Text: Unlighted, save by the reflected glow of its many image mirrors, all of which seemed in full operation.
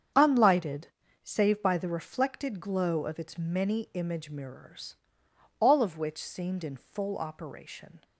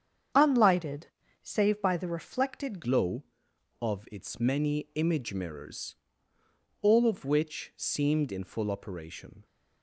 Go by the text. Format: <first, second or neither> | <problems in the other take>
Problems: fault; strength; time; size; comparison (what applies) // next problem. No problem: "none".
first | starts louder than the rest; strong; until 1.6 s; 8 dB; strong in the first // changes voice at "glow"; from 2.8 s on; 6.6 s long